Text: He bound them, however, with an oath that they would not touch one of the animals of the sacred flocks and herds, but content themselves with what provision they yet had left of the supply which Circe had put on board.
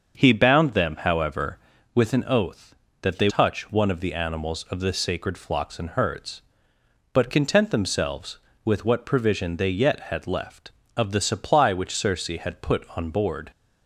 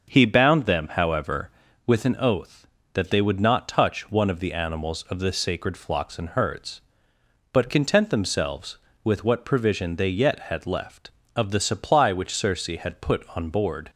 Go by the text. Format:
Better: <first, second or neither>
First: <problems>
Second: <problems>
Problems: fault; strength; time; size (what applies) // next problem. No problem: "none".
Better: second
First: starts louder than the rest; until 1.2 s; 6.5 dB // skips "would not"; at 3.2 s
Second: starts louder than the rest; until 1.1 s; 6.5 dB